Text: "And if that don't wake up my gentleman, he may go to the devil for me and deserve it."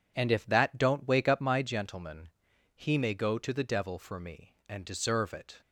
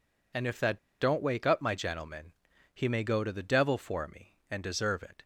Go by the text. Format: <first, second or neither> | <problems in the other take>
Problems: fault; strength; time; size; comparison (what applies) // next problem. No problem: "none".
first | pauses between "that" and "don't"; slight; at 0.7 s; 0.21 s long